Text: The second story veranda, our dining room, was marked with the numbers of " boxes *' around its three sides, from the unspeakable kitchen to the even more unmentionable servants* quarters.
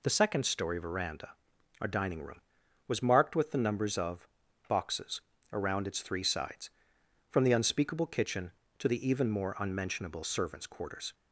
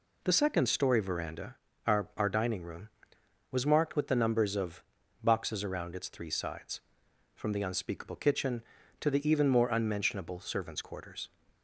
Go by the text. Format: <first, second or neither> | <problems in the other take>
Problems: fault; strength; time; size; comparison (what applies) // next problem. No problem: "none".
first | says "our" twice; at 2.1 s